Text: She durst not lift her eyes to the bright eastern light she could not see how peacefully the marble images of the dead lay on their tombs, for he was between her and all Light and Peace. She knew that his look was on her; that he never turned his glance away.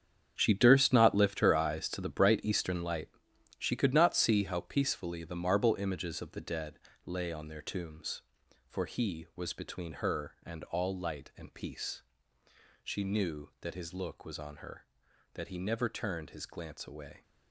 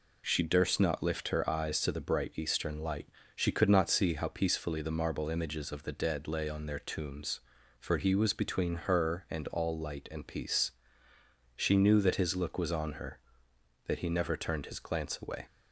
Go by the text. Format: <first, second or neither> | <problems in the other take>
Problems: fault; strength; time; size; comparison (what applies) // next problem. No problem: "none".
second | gets quieter; strong; throughout; 12 dB // pauses between "light" and "she"; noticeable; at 3.0 s; 0.50 s long; slight in the second // pauses between "dead" and "lay"; slight; at 6.7 s; 0.28 s long